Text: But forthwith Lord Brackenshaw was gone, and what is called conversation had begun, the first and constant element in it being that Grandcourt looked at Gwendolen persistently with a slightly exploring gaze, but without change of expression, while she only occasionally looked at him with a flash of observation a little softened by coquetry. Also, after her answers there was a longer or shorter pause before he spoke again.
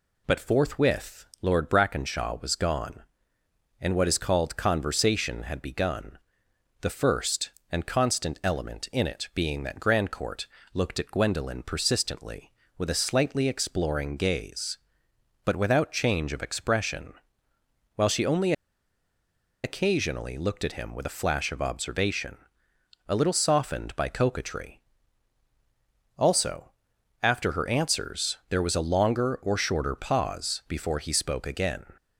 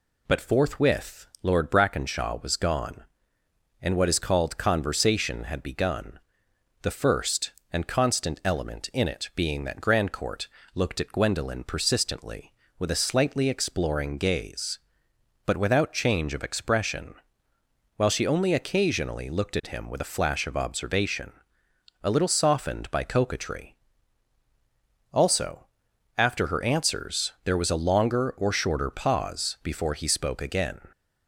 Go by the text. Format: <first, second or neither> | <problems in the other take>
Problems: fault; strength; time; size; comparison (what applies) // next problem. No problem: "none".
second | pauses between "forthwith" and "Lord"; slight; at 1.2 s; 0.16 s long; slight in the second // pauses between "Grandcourt" and "looked"; slight; at 10.4 s; 0.26 s long; slight in the second // pauses between "only" and "occasionally"; at 18.5 s; 1.1 s long // pauses between "observation" and "a"; noticeable; at 22.3 s; 0.70 s long; noticeable in the second